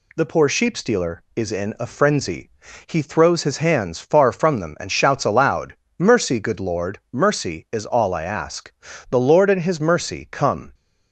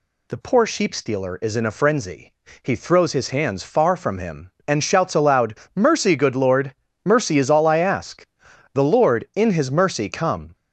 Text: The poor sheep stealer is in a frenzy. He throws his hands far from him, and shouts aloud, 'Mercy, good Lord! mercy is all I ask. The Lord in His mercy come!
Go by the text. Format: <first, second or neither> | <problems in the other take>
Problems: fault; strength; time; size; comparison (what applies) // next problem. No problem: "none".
second | says "them" for "him"; at 4.5 s